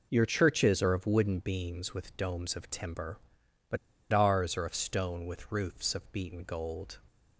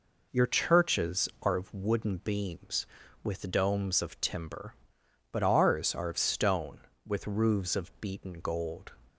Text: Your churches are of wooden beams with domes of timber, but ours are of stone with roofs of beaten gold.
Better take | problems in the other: second | pauses between "but" and "ours"; slight; at 3.7 s; 0.34 s long

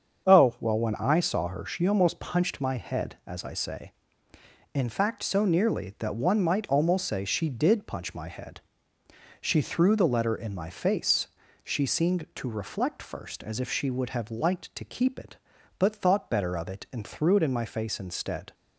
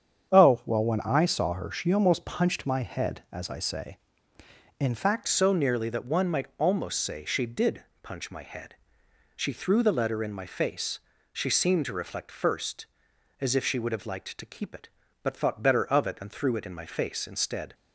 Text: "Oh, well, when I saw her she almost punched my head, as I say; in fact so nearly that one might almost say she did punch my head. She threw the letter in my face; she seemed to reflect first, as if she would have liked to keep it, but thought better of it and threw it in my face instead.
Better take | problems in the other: first | starts louder than the rest; strong; until 1.3 s; 8 dB; strong in the first // changes voice at "so"; from 5.2 s on; 12.5 s long // pauses between "did" and "punch"; slight; at 7.8 s; 0.18 s long

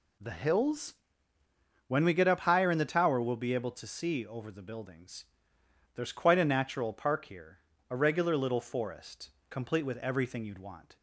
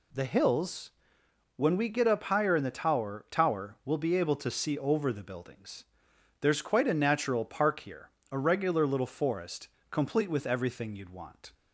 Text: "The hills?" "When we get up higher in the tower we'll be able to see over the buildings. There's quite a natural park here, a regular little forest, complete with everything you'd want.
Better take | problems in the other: first | says "tower" twice; at 3.3 s

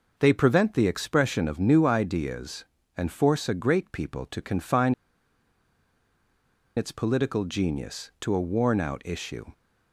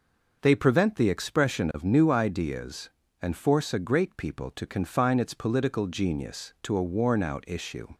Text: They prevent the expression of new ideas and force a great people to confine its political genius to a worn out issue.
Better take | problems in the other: second | pauses between "confine" and "its"; strong; at 4.9 s; 1.8 s long

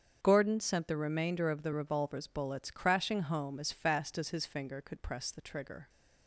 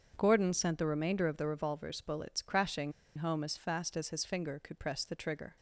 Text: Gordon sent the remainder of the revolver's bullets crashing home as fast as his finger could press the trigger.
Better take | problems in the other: first | starts louder than the rest; until 1.1 s; 7 dB; strong in the first // pauses between "crashing" and "home"; slight; at 2.9 s; 0.25 s long

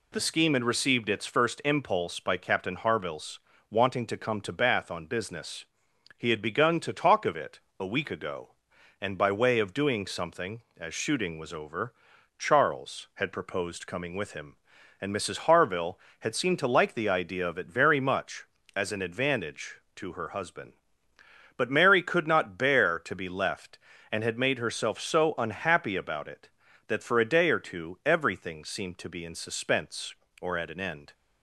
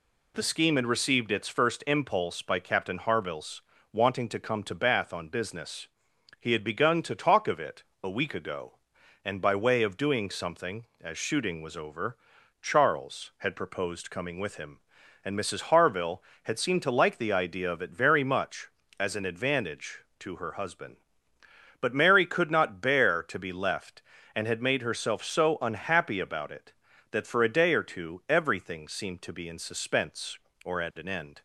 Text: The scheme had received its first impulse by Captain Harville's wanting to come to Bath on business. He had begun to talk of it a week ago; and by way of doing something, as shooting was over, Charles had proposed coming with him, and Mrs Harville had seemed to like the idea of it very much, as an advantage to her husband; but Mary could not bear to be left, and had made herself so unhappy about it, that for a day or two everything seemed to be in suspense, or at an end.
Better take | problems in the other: neither | pauses between "Harville's" and "wanting"; slight; the same in both // pauses between "it" and "a"; slight; the same in both

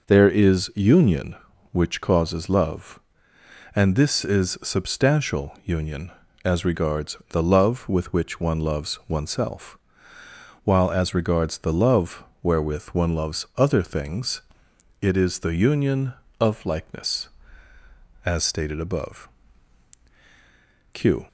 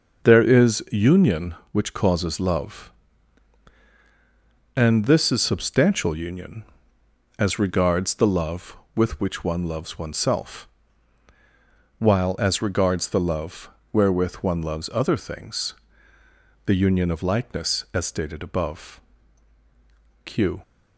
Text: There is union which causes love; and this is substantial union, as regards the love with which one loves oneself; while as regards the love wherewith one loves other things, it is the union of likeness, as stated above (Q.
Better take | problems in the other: first | starts louder than the rest; until 1.3 s; 6.5 dB // pauses between "love" and "wherewith"; slight; at 13.6 s; 0.24 s long; slight in the first // skips "it is"; at 16.1 s

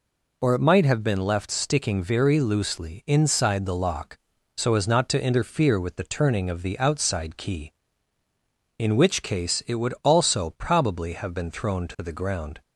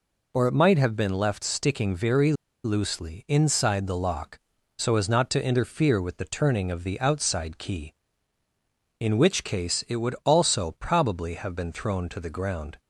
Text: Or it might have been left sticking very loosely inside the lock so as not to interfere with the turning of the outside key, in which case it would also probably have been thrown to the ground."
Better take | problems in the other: first | pauses between "very" and "loosely"; slight; at 2.3 s; 0.31 s long

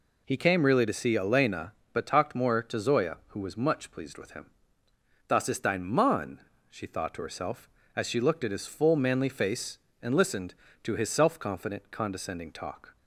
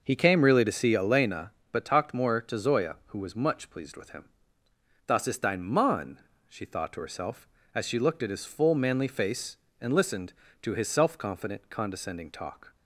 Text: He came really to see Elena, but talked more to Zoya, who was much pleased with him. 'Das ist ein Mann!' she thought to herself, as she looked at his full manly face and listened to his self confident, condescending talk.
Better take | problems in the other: first | starts louder than the rest; noticeable; until 1.2 s; 5.5 dB

